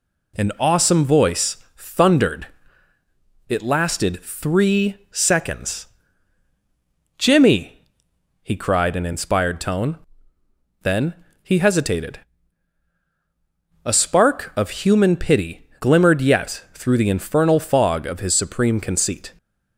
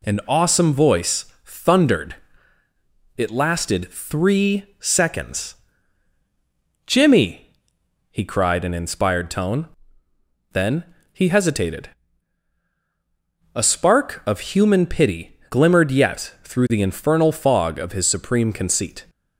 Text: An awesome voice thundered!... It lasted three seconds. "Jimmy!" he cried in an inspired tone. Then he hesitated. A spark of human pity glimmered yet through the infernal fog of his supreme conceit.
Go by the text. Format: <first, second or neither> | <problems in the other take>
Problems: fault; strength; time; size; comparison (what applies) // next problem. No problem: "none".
neither | pauses between "voice" and "thundered"; slight; the same in both // pauses between "three" and "seconds"; slight; the same in both // pauses between "Then" and "he"; slight; the same in both